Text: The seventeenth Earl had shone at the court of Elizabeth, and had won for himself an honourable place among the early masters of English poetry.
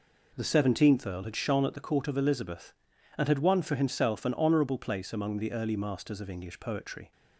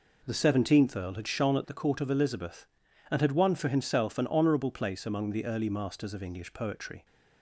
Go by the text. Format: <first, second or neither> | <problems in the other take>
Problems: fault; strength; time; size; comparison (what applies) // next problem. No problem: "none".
neither | none